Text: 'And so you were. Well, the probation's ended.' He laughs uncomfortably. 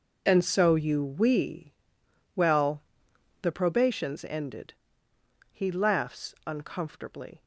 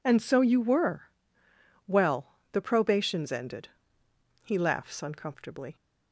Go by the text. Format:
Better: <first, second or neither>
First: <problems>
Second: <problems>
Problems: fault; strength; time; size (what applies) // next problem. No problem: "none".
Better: second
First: says "we" for "were"; at 1.0 s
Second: none